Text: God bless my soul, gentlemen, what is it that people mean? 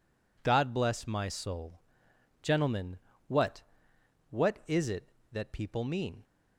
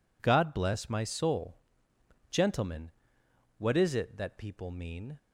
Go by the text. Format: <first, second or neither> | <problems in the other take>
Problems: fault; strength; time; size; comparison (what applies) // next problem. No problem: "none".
second | says "what" twice; at 4.2 s